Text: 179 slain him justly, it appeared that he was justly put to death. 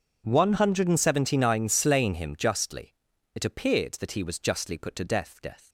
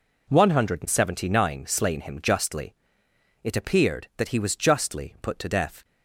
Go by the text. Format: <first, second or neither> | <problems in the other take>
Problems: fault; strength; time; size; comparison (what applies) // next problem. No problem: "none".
second | says "death" twice; at 5.4 s